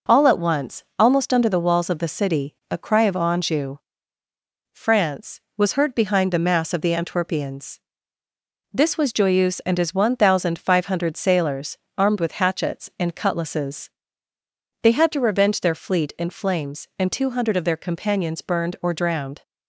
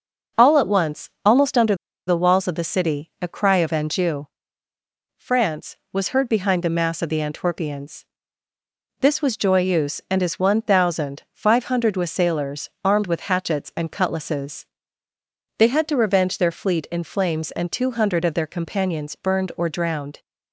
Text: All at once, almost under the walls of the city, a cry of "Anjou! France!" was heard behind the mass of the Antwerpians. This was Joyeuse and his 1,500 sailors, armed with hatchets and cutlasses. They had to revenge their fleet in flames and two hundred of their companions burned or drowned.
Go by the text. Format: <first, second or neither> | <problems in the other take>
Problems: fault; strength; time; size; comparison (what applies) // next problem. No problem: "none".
first | starts louder than the rest; noticeable; until 1.4 s; 6 dB // pauses between "under" and "the"; slight; at 1.7 s; 0.32 s long